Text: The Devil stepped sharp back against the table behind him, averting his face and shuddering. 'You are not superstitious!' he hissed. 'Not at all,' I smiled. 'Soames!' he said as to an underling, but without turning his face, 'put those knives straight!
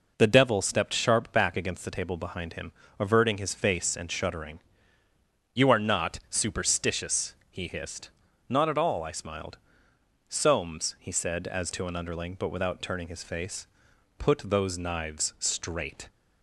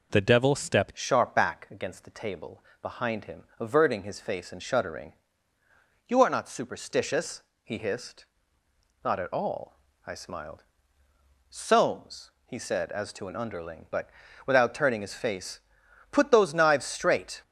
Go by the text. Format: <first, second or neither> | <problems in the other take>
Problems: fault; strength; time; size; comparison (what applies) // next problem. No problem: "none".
first | changes voice at "sharp"; from 0.9 s on; 16.5 s long // pauses between "table" and "behind"; slight; at 2.6 s; 0.18 s long // pauses between "but" and "without"; at 14.0 s; 0.38 s long